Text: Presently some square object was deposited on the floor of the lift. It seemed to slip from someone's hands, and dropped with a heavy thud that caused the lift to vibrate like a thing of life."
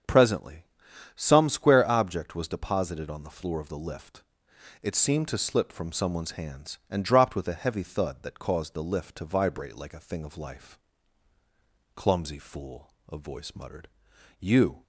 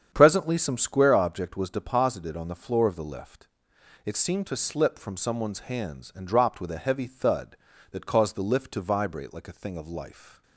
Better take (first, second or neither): second